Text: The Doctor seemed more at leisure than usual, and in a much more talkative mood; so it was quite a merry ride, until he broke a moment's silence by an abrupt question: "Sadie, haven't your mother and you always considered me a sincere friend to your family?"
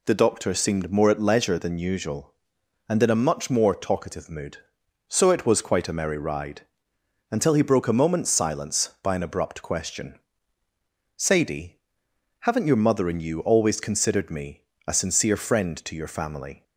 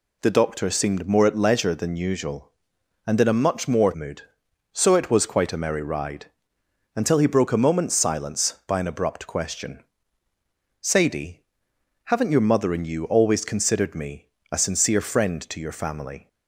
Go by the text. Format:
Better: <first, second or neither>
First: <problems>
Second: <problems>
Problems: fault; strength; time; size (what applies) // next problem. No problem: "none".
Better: first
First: pauses between "me" and "a"; slight; at 14.6 s; 0.24 s long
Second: skips "talkative"; at 3.9 s // pauses between "me" and "a"; slight; at 14.2 s; 0.24 s long